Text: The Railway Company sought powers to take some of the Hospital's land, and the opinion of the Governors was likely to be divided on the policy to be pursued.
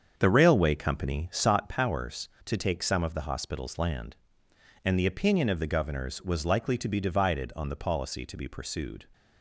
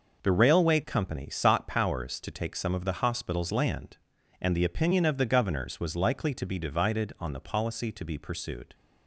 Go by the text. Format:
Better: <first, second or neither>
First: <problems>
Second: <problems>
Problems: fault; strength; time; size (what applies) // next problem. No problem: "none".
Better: second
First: starts louder than the rest; strong; until 1.5 s; 7 dB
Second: none